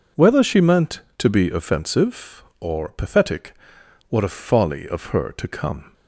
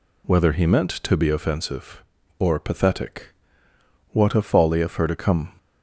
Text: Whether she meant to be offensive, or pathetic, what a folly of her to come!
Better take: first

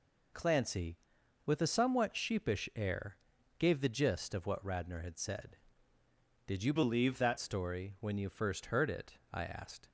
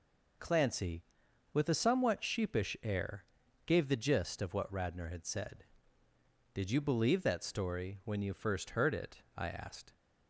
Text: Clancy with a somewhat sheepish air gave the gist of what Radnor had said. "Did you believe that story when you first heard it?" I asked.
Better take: second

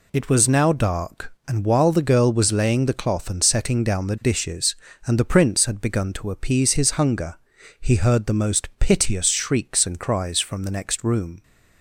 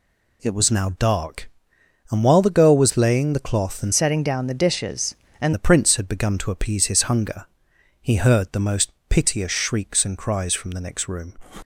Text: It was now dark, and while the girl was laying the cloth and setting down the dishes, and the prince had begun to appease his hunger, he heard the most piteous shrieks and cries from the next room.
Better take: first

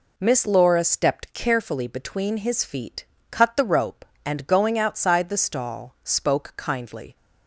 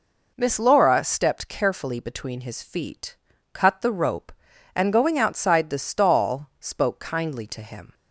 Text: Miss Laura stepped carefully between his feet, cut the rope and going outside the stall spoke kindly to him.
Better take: second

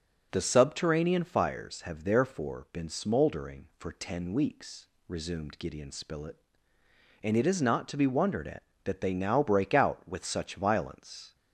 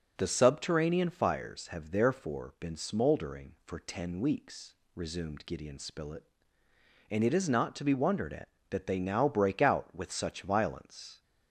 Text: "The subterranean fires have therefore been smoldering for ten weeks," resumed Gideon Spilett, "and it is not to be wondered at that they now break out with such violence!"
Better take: neither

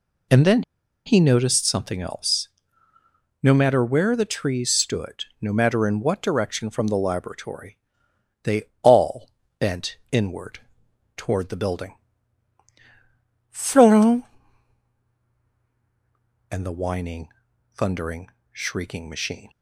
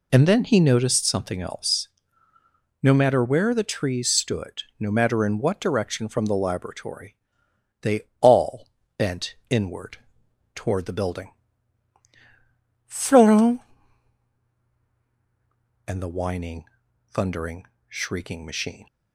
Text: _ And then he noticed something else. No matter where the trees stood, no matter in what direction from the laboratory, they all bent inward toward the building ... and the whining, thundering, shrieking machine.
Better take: second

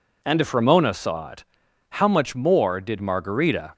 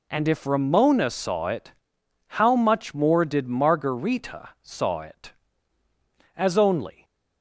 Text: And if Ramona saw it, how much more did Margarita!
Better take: first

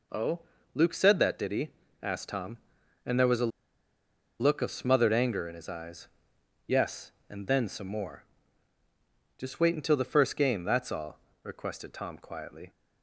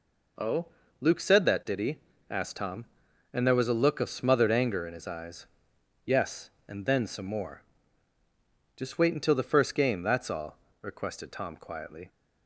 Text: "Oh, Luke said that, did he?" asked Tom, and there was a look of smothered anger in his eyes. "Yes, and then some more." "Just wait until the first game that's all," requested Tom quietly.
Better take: second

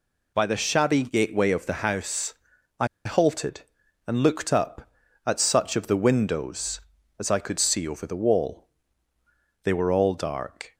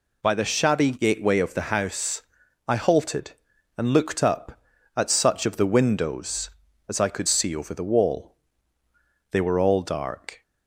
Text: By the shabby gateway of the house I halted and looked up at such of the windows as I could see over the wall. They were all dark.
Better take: second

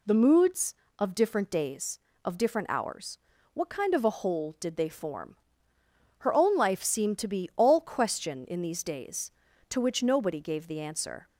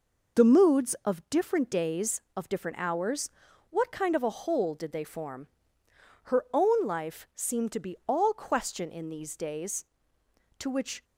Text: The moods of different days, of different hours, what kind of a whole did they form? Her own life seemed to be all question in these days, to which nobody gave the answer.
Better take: first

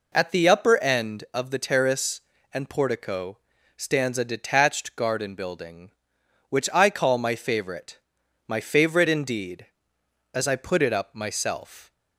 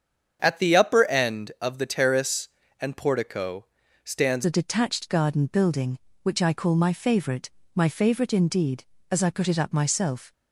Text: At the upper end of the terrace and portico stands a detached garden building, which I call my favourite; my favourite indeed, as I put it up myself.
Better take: first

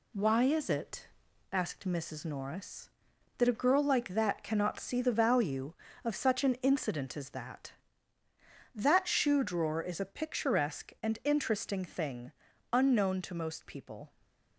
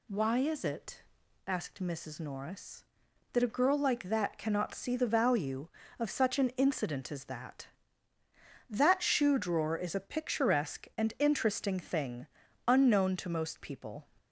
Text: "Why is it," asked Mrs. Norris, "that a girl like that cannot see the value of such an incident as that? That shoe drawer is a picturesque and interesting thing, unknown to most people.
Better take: second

